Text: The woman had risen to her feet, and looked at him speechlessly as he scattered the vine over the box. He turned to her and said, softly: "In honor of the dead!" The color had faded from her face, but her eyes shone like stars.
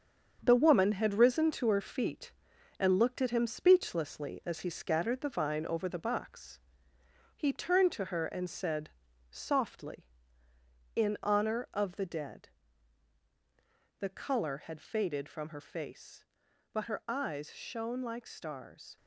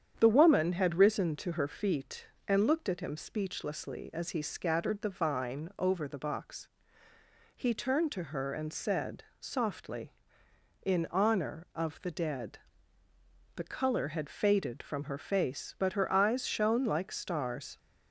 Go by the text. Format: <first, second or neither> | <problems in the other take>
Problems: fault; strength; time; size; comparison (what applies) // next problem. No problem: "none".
second | gets quieter; strong; throughout; 7.5 dB // starts louder than the rest; strong; until 1.4 s; 7 dB; strong in the second